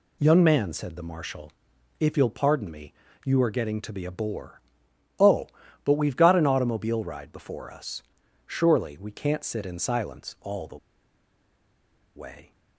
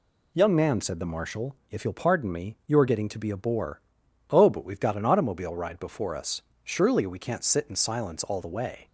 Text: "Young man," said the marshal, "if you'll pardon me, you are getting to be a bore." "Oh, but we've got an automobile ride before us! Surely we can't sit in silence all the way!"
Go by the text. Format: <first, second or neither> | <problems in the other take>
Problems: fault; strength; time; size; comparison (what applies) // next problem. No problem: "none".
second | pauses between "the" and "way"; strong; at 10.7 s; 1.3 s long